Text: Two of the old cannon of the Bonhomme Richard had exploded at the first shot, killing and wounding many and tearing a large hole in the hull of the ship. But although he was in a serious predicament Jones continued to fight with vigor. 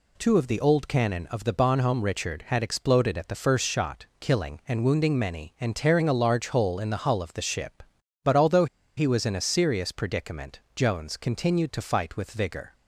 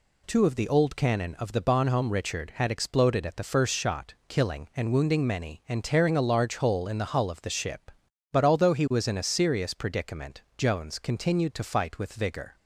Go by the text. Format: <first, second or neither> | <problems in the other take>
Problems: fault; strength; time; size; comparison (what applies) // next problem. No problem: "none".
second | pauses between "although" and "he"; slight; at 8.6 s; 0.31 s long // pauses between "predicament" and "Jones"; slight; at 10.6 s; 0.16 s long; slight in the second